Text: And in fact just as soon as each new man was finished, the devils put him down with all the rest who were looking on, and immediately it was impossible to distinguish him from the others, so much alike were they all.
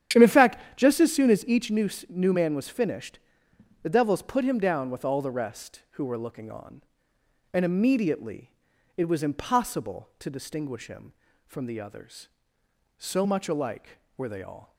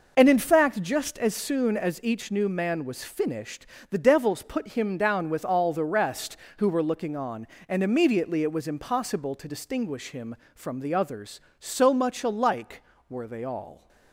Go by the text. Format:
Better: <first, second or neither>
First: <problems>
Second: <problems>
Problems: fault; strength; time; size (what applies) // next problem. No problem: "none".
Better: second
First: starts louder than the rest; strong; until 1.3 s; 10.5 dB // pauses between "fact" and "just"; slight; at 0.5 s; 0.18 s long // says "new" twice; at 2.0 s // pauses between "immediately" and "it"; noticeable; at 8.4 s; 0.48 s long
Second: none